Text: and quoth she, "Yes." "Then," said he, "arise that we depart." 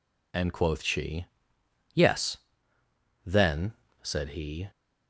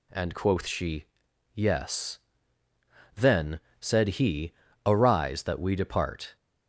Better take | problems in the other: second | stops before "arise that we depart"; at 4.7 s

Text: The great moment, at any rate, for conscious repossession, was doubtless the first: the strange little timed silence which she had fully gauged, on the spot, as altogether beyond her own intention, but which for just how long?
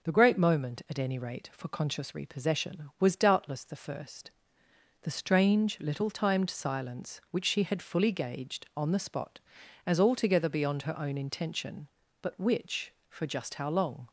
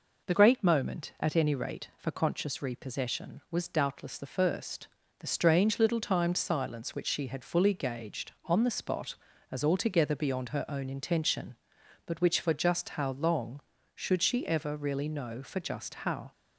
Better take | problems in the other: first | goes on to say "should she ever really know for just how"; strong; from 13.9 s on; 2.3 s long

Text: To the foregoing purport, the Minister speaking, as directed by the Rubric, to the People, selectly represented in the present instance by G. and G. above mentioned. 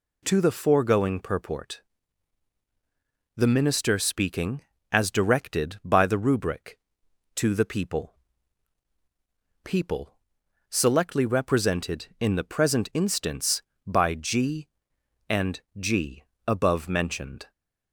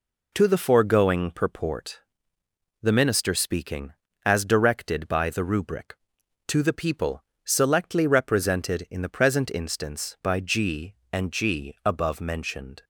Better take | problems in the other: second | says "People" twice; at 9.6 s // pauses between "and" and "G"; slight; at 15.5 s; 0.20 s long

